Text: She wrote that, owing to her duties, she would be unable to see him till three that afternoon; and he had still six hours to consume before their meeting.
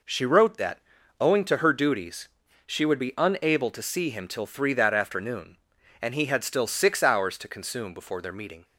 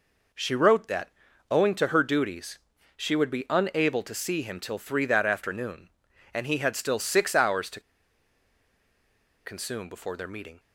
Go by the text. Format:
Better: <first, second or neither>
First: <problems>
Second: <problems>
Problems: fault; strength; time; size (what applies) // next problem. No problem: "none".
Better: first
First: none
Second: pauses between "to" and "consume"; strong; at 7.8 s; 1.6 s long